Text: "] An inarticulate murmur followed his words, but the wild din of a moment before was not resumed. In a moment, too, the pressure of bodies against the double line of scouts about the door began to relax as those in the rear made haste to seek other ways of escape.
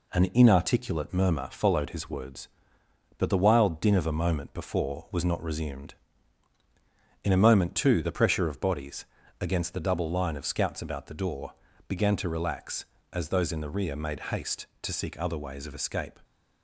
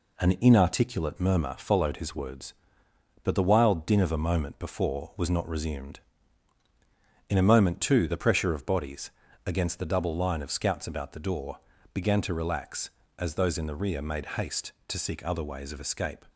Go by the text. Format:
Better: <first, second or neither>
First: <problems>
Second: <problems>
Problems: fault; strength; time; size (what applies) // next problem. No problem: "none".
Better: neither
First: pauses between "bodies" and "against"; slight; at 9.0 s; 0.34 s long // pauses between "door" and "began"; slight; at 11.5 s; 0.34 s long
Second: pauses between "bodies" and "against"; slight; at 9.1 s; 0.34 s long // pauses between "door" and "began"; slight; at 11.5 s; 0.34 s long